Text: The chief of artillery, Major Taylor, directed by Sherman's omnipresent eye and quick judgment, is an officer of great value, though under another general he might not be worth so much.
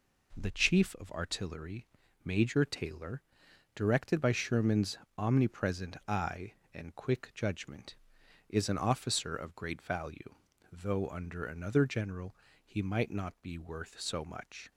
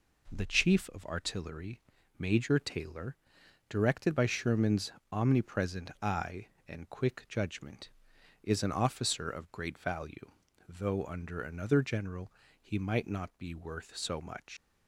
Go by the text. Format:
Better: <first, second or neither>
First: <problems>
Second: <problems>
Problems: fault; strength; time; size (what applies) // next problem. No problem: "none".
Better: first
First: pauses between "Sherman's" and "omnipresent"; slight; at 4.9 s; 0.22 s long // pauses between "general" and "he"; slight; at 12.3 s; 0.30 s long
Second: pauses between "Sherman's" and "omnipresent"; slight; at 4.9 s; 0.22 s long // pauses between "general" and "he"; slight; at 12.3 s; 0.30 s long // leaves "much" unfinished; at 14.5 s; 95 ms